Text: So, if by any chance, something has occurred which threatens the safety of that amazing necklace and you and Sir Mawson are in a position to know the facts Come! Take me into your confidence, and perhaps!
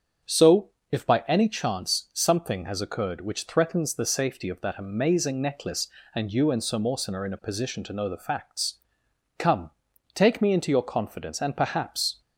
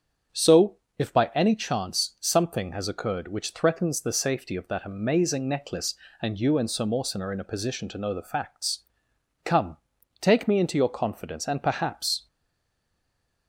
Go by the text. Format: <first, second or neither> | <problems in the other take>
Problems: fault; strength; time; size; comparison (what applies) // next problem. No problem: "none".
first | starts louder than the rest; strong; until 1.5 s; 7.5 dB; also in the first // pauses between "facts" and "Come"; noticeable; at 8.7 s; 0.63 s long; noticeable in the first // stays silent after the last word; noticeable; from 12.2 s on; 1.2 s long